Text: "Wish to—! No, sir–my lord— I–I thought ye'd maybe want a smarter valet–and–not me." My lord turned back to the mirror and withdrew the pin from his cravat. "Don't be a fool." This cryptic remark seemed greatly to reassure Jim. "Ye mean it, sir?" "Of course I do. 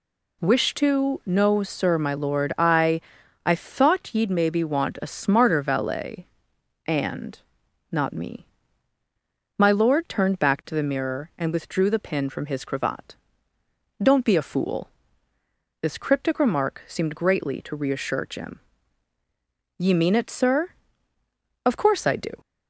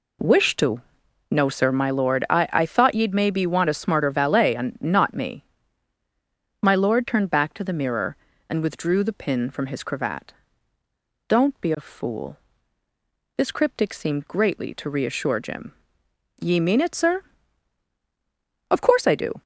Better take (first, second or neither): first